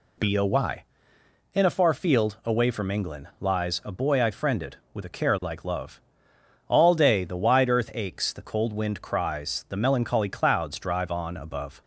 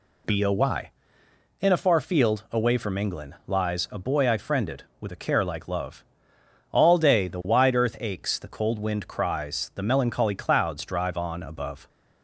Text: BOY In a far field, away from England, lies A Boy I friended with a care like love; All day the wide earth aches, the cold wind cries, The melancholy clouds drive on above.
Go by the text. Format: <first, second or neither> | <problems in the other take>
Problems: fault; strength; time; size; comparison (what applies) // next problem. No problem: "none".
neither | none